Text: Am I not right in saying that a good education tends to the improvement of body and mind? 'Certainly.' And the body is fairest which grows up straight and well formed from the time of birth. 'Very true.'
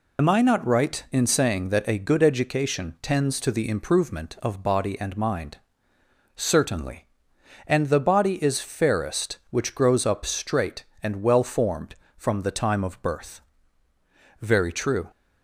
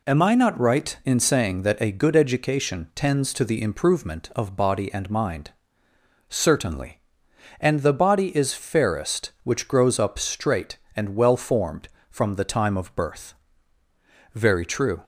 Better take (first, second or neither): second